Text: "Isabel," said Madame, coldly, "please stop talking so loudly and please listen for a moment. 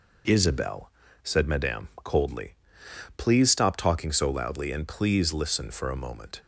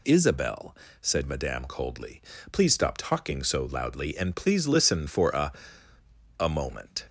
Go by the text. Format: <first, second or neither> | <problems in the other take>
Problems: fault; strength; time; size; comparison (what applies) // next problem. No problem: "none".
first | says "a" twice; at 6.3 s